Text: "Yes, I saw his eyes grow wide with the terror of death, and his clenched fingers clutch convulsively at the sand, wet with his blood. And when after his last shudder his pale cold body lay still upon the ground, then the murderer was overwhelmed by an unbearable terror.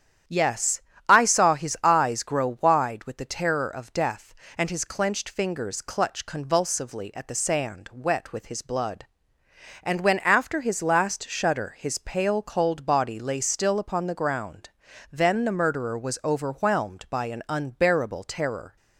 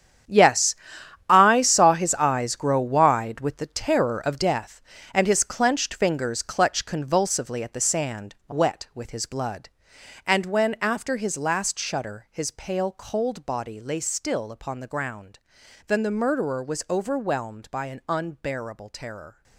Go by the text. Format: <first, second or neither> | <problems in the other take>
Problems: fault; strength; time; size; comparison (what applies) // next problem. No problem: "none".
first | gets quieter; strong; throughout; 14 dB // starts louder than the rest; strong; until 1.8 s; 9 dB; strong in the first